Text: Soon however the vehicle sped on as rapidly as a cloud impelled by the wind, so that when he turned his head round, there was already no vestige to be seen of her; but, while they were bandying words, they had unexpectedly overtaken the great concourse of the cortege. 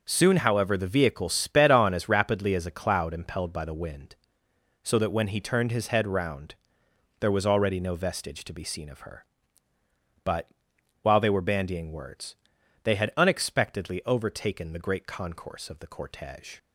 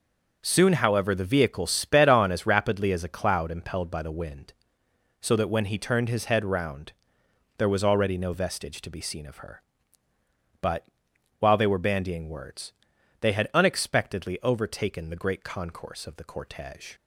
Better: neither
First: none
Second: none

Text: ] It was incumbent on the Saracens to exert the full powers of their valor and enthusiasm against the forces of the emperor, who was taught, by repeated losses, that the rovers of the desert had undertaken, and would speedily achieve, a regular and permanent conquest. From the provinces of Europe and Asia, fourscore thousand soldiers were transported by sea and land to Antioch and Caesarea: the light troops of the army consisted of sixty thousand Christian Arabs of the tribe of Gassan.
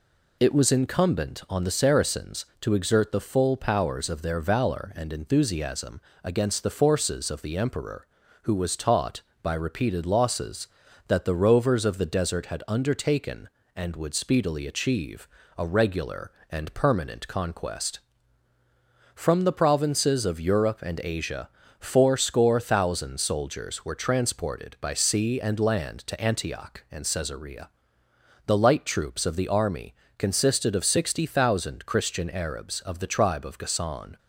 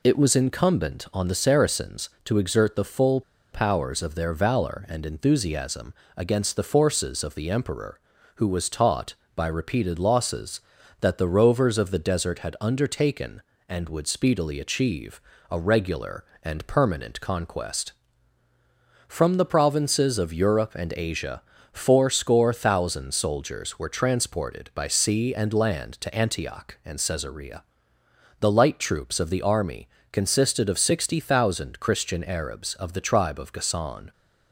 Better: first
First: pauses between "enthusiasm" and "against"; slight; at 5.9 s; 0.24 s long // pauses between "army" and "consisted"; slight; at 29.9 s; 0.24 s long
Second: pauses between "full" and "powers"; slight; at 3.2 s; 0.31 s long // pauses between "enthusiasm" and "against"; slight; at 5.9 s; 0.24 s long // pauses between "army" and "consisted"; slight; at 29.8 s; 0.24 s long

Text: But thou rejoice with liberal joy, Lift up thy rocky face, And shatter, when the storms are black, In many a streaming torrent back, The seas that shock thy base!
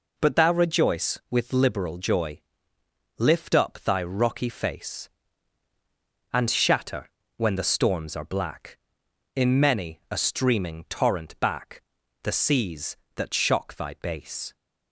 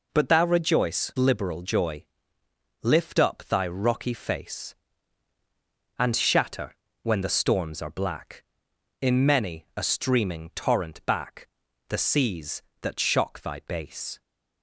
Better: first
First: none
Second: skips "with"; at 1.1 s

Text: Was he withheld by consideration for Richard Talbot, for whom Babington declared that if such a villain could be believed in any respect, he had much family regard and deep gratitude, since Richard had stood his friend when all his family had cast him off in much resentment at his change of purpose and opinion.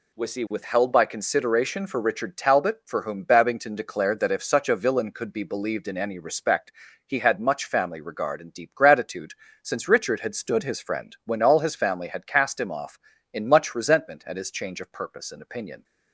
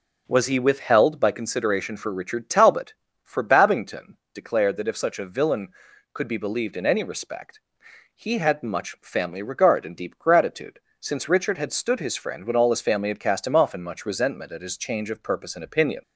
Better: first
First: none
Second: skips "whom"; at 3.4 s // pauses between "Babington" and "declared"; slight; at 4.1 s; 0.18 s long

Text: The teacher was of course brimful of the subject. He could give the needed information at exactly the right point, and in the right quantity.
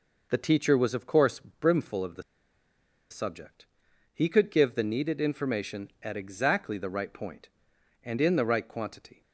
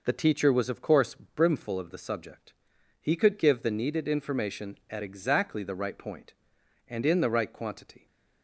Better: second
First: pauses between "the" and "subject"; noticeable; at 2.2 s; 0.88 s long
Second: none

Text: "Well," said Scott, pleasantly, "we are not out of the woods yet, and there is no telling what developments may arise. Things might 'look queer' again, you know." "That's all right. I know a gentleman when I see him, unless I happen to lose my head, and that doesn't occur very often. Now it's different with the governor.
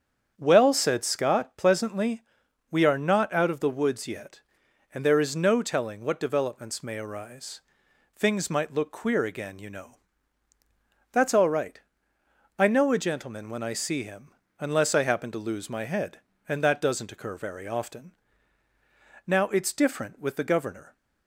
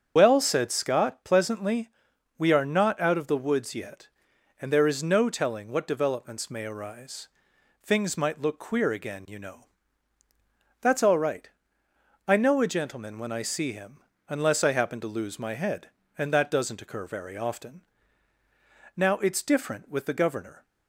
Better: first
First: starts louder than the rest; strong; until 1.3 s; 8 dB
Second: loses the start of "Well"; at 0.1 s; 110 ms // starts louder than the rest; strong; until 1.1 s; 8 dB

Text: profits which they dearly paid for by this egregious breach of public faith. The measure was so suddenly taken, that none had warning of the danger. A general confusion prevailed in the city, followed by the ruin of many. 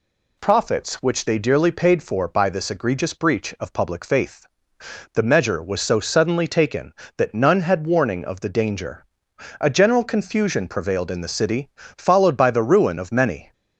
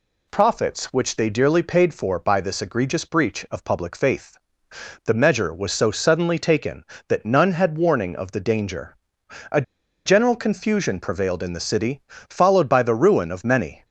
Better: first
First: none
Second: pauses between "A" and "general"; at 9.6 s; 0.43 s long

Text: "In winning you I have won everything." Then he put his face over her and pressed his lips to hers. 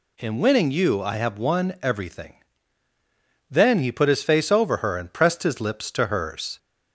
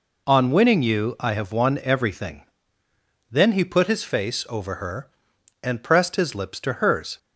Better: first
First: none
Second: says "On" for "In"; at 0.2 s

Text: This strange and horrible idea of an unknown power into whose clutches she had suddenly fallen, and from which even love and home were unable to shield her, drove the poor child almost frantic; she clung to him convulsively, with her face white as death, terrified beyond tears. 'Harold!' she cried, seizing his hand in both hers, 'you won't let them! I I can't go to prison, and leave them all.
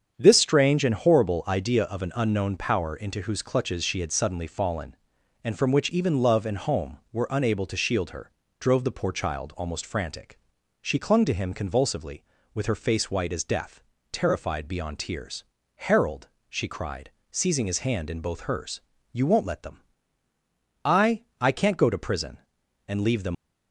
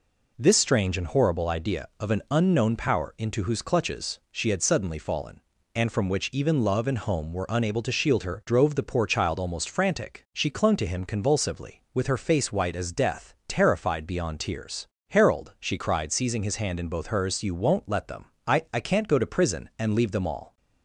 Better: second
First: starts louder than the rest; strong; until 1.1 s; 7.5 dB // pauses between "I" and "I"; slight; at 21.2 s; 0.16 s long // stops before "all"; at 23.3 s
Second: none

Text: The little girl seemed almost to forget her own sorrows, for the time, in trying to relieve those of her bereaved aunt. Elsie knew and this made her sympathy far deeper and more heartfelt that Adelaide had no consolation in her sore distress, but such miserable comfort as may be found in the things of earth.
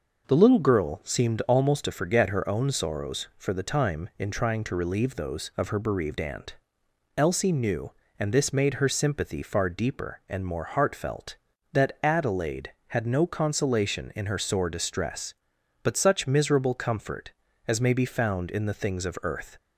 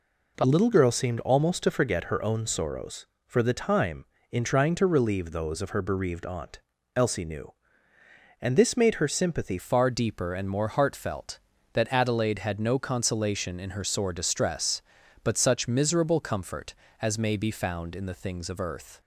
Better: first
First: none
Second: changes voice at "far"; from 9.5 s on; 9.5 s long

